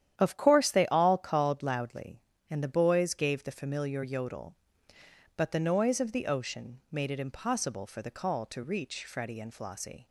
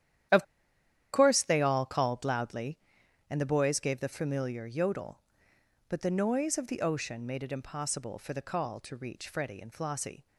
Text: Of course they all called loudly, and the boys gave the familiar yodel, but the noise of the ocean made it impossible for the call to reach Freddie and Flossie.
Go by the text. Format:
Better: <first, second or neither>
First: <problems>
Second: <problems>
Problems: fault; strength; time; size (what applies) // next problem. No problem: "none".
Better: first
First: starts louder than the rest; strong; until 1.1 s; 10.5 dB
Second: starts louder than the rest; strong; until 2.0 s; 11 dB // pauses between "Of" and "course"; noticeable; at 0.4 s; 0.69 s long